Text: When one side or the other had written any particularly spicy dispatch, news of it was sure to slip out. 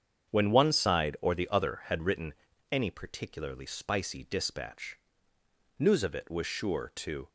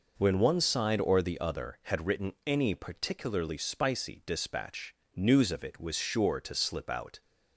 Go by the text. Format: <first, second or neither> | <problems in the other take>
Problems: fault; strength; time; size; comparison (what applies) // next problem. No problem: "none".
second | starts louder than the rest; strong; until 1.3 s; 8 dB // pauses between "written" and "any"; at 2.3 s; 0.38 s long // stops before "slip out"; at 7.2 s